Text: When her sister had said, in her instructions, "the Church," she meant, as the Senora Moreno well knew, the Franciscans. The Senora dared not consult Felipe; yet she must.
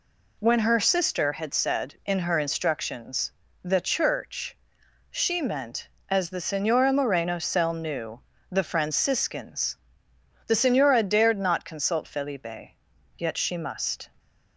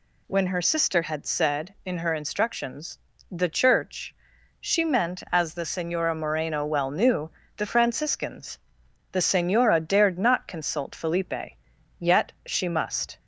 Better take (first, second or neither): second